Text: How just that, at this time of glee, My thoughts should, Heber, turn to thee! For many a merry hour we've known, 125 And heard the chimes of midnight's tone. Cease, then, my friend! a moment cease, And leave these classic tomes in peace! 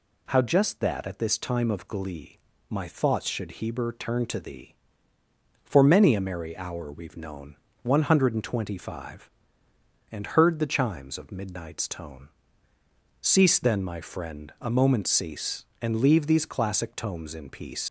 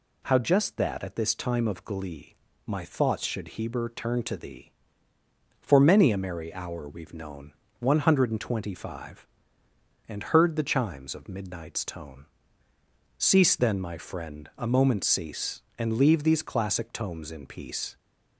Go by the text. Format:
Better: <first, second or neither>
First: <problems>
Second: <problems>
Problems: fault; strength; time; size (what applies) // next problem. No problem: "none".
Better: second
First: leaves "peace" unfinished; at 17.8 s; 125 ms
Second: none